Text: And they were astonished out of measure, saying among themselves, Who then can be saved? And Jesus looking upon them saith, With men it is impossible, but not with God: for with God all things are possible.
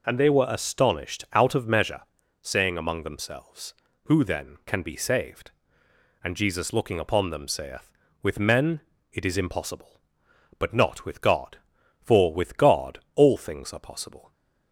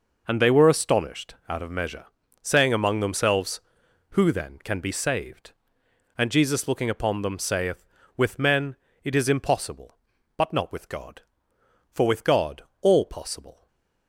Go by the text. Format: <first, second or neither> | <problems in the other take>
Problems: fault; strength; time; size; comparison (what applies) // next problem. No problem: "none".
first | pauses between "men" and "it"; slight; at 8.7 s; 0.28 s long; slight in the first // pauses between "God" and "all"; slight; at 12.6 s; 0.18 s long; slight in the first // skips "things are"; at 13.0 s // stays silent after the last word; slight; from 13.5 s on; 0.5 s long; slight in the first